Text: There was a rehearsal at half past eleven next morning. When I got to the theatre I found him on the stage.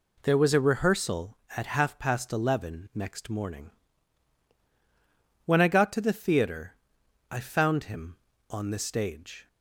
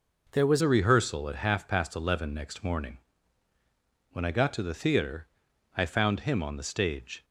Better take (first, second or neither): first